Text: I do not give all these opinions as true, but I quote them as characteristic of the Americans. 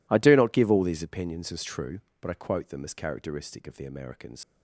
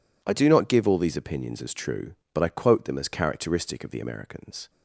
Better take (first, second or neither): second